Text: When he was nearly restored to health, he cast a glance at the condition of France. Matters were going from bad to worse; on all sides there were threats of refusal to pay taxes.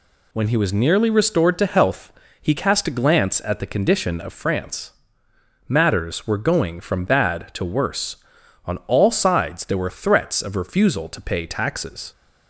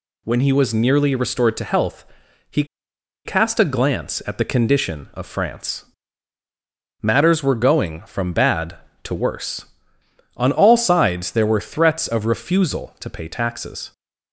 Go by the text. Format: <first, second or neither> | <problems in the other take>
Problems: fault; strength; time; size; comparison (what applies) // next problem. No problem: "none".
first | pauses between "he" and "cast"; noticeable; at 2.6 s; 0.60 s long